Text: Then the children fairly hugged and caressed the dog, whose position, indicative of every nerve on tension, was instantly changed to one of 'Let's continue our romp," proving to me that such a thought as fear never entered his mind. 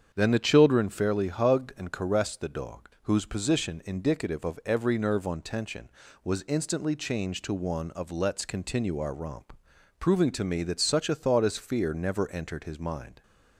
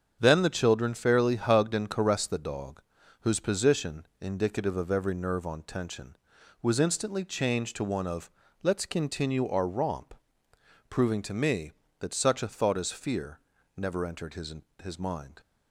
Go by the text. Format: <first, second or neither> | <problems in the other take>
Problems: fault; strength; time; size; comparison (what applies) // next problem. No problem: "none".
first | starts louder than the rest; strong; until 1.2 s; 7.5 dB; strong in the first // pauses between "of" and "Let's"; slight; at 8.2 s; 0.32 s long // pauses between "fear" and "never"; at 13.3 s; 0.38 s long // says "his" twice; at 14.8 s